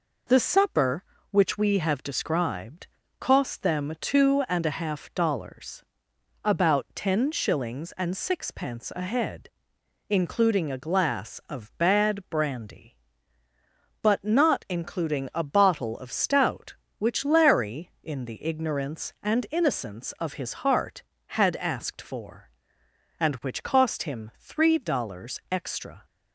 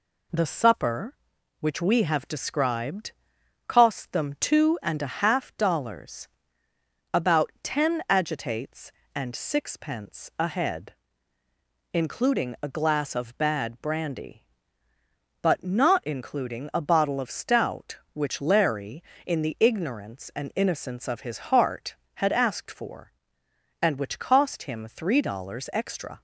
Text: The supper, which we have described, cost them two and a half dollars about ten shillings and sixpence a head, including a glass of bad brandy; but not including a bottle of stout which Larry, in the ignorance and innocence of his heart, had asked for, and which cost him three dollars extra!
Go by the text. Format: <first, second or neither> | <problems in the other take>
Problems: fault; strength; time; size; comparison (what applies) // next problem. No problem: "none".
first | pauses between "dollars" and "about"; noticeable; at 6.2 s; 0.84 s long; noticeable in the first // says "agitates" for "shillings"; at 8.0 s